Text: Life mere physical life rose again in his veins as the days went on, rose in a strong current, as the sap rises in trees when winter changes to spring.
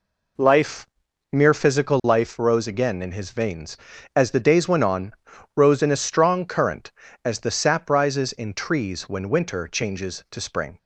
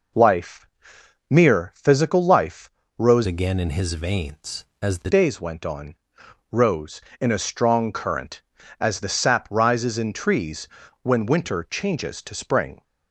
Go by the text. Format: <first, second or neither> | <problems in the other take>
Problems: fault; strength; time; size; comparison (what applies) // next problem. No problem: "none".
first | pauses between "Life" and "mere"; noticeable; at 0.6 s; 0.60 s long; noticeable in the first // pauses between "life" and "rose"; slight; at 2.7 s; 0.28 s long // changes voice from "again" to "the"; from 3.2 to 5.0 s; 1.8 s long // pauses between "trees" and "when"; slight; at 10.6 s; 0.34 s long